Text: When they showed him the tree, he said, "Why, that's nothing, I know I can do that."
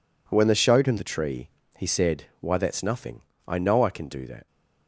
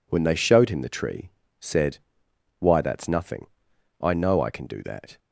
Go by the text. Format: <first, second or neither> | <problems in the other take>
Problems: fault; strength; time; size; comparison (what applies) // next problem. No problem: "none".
first | skips "he"; at 1.4 s